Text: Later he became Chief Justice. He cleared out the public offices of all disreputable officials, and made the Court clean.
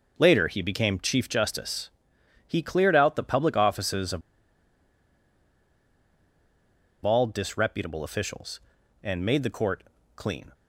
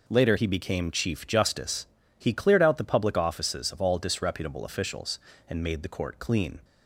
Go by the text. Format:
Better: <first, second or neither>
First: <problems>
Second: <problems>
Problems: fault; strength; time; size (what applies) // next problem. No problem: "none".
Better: second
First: pauses between "of" and "all"; strong; at 4.2 s; 2.8 s long // pauses between "Court" and "clean"; slight; at 9.8 s; 0.32 s long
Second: none